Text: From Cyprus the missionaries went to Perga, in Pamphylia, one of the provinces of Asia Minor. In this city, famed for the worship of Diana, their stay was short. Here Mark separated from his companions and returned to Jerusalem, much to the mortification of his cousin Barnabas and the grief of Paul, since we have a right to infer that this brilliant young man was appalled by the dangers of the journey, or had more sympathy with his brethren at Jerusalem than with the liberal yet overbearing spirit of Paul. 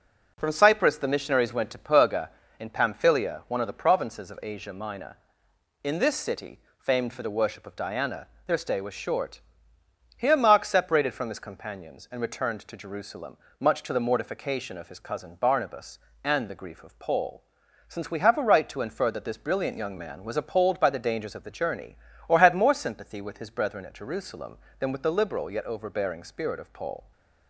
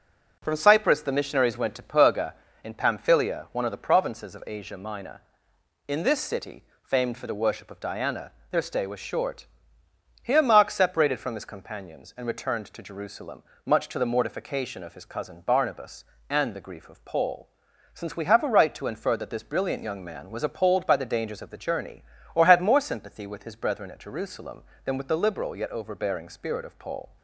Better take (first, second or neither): neither